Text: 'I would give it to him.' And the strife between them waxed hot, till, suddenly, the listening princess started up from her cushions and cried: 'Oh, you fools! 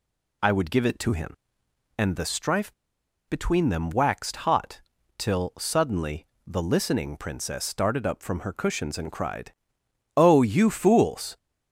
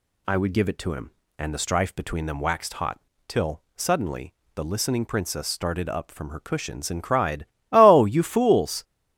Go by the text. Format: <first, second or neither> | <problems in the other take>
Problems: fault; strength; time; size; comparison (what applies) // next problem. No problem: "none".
second | pauses between "strife" and "between"; noticeable; at 2.7 s; 0.54 s long